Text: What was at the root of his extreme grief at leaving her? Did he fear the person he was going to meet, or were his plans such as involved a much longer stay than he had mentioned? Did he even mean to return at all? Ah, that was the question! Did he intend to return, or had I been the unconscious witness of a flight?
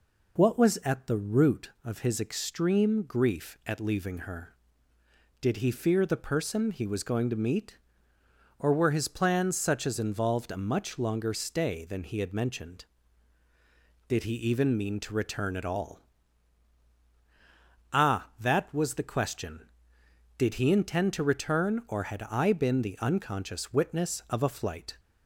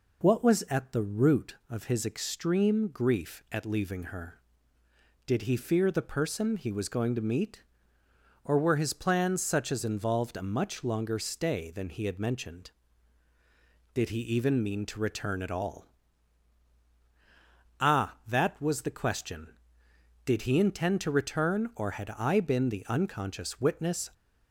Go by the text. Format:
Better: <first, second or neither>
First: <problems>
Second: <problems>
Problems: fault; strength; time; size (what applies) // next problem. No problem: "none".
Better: first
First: none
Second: stops before "of a flight"; at 24.1 s